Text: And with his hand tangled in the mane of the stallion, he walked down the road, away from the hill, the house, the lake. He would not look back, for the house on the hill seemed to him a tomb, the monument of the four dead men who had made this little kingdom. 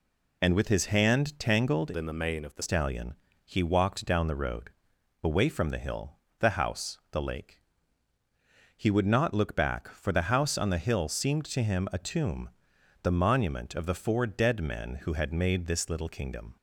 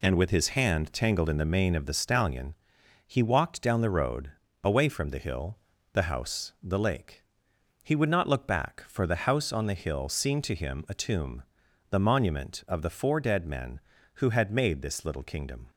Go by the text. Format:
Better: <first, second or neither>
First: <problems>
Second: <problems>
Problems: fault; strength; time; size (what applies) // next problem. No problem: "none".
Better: second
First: changes voice from "in" to "the"; from 1.9 to 2.6 s; 0.7 s long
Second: none